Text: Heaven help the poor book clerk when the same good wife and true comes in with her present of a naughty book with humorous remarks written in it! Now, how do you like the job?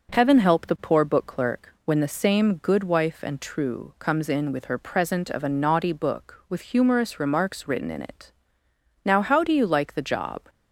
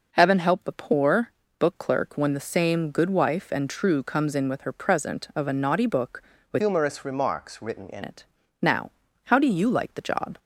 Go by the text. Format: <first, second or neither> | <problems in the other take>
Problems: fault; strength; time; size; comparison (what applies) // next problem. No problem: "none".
first | pauses between "poor" and "book"; slight; at 1.3 s; 0.28 s long // changes voice from "humorous" to "in"; from 6.5 to 8.0 s; 1.5 s long